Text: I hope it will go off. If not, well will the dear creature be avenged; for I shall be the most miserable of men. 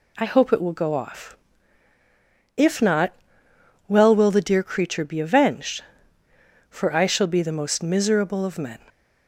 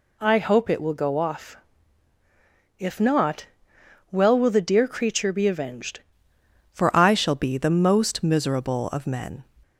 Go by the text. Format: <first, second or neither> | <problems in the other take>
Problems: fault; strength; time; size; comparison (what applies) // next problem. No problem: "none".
first | changes voice at "for"; from 6.7 s on; 2.7 s long